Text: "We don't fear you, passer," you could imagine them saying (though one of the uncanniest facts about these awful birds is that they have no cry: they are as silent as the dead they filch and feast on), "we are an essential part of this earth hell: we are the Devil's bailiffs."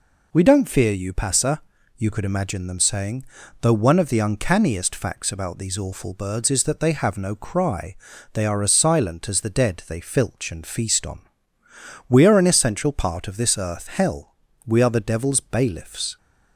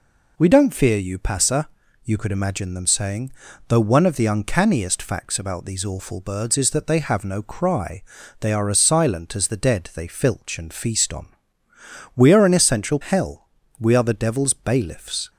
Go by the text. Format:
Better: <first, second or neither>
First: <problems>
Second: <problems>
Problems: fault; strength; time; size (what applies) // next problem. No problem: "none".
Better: first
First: none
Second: skips "part of this earth"; at 13.0 s